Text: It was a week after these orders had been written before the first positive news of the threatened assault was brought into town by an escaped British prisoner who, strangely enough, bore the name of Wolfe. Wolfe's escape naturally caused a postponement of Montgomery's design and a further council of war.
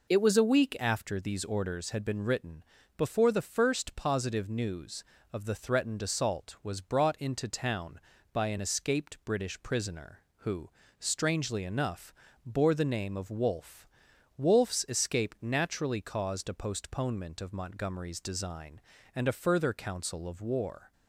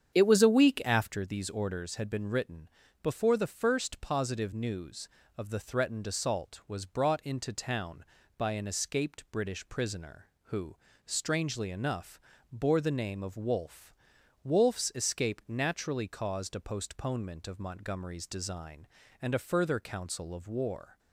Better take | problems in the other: first | starts louder than the rest; strong; until 1.2 s; 8.5 dB // pauses between "written" and "before"; slight; at 2.6 s; 0.32 s long; slight in the first

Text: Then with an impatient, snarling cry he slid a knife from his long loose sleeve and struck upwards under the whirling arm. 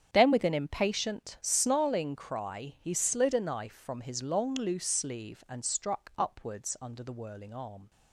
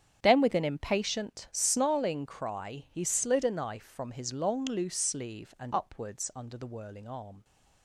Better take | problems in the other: first | starts louder than the rest; strong; until 1.2 s; 8 dB; strong in the first // skips "struck"; at 5.7 s

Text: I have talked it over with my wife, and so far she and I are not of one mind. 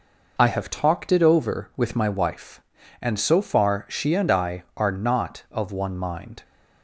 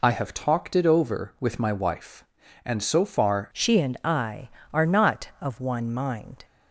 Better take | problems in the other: first | changes voice at "she"; from 3.5 s on; 2.9 s long

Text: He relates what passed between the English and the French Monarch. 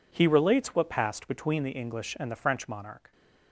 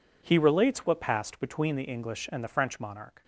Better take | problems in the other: neither | none

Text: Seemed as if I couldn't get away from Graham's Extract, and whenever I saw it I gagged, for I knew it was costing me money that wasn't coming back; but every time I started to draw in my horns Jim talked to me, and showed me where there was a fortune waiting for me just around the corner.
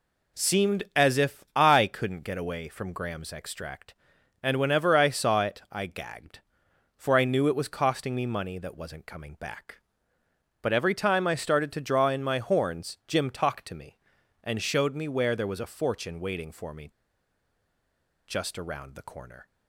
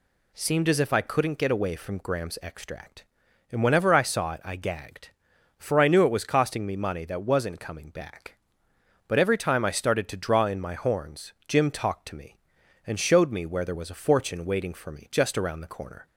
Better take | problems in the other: second | pauses between "me" and "just"; strong; at 16.8 s; 1.3 s long

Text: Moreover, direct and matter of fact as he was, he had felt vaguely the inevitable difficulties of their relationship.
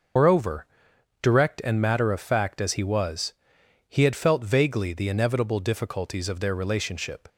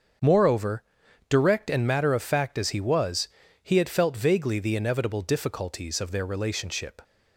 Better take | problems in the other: second | loses the start of "Moreover"; at 0.1 s; 140 ms // starts louder than the rest; noticeable; until 1.7 s; 6 dB; also in the second

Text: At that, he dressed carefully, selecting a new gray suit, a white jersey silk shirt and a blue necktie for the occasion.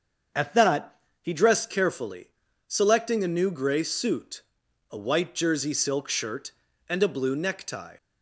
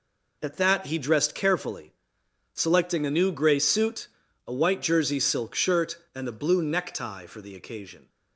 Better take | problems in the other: second | starts louder than the rest; until 1.6 s; 7 dB // stops before "for the occasion"; at 7.9 s

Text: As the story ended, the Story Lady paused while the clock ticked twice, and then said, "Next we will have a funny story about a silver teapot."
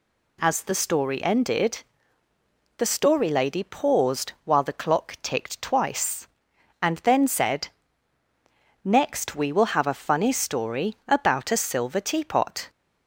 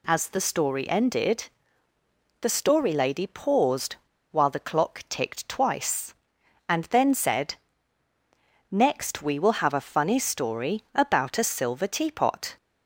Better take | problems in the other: first | pauses between "paused" and "while"; slight; at 3.9 s; 0.35 s long

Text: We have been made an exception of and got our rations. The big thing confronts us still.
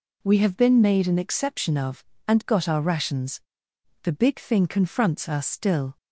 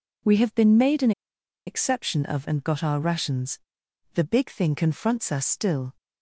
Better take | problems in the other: first | pauses between "an" and "exception"; noticeable; at 1.1 s; 0.55 s long

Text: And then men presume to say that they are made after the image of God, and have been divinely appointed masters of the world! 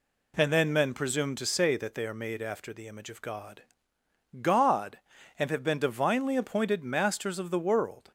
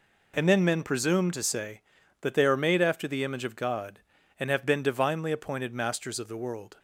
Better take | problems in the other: second | says "God" twice; at 4.4 s

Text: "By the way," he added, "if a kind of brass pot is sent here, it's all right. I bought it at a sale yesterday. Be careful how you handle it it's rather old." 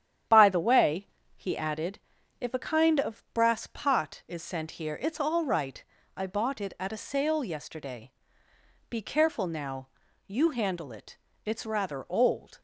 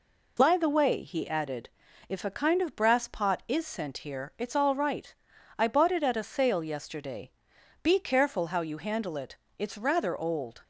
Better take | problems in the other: second | starts louder than the rest; strong; until 1.5 s; 9.5 dB // says "now" for "how"; at 9.4 s // pauses between "it" and "it's"; slight; at 11.1 s; 0.26 s long; slight in the second

